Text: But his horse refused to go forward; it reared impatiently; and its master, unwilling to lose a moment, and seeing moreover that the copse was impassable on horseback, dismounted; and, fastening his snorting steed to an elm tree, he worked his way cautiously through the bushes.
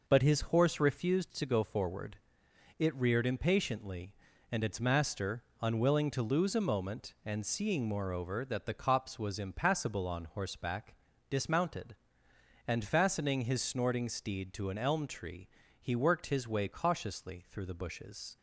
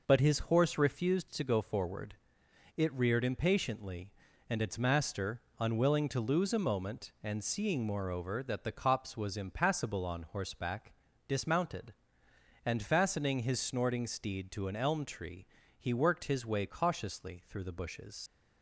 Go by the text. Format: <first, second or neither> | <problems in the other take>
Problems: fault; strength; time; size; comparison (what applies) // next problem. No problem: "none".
first | leaves "bushes" unfinished; at 18.2 s; 85 ms